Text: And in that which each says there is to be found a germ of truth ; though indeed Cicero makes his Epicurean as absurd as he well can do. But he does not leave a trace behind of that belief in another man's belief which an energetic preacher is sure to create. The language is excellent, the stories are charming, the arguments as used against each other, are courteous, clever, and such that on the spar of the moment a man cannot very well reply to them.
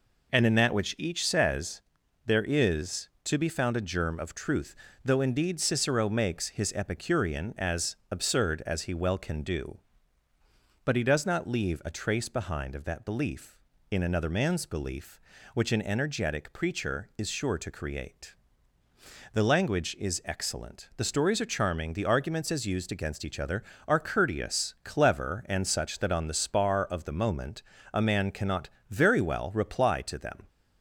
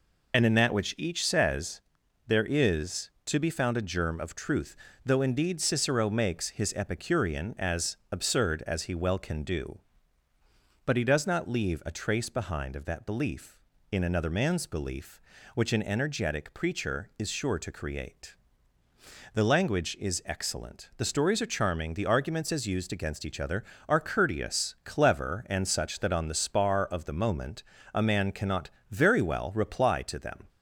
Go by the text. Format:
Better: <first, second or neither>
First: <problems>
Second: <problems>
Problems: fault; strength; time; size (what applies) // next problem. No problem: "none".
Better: first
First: pauses between "says" and "there"; at 1.8 s; 0.44 s long // pauses between "as" and "absurd"; slight; at 7.9 s; 0.16 s long // pauses between "moment" and "a"; slight; at 27.6 s; 0.30 s long // pauses between "cannot" and "very"; slight; at 28.6 s; 0.20 s long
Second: loses the start of "And"; at 0.3 s; 35 ms // pauses between "says" and "there"; noticeable; at 1.8 s; 0.46 s long // pauses between "as" and "absurd"; slight; at 7.9 s; 0.16 s long // pauses between "moment" and "a"; slight; at 27.6 s; 0.30 s long // pauses between "cannot" and "very"; slight; at 28.6 s; 0.20 s long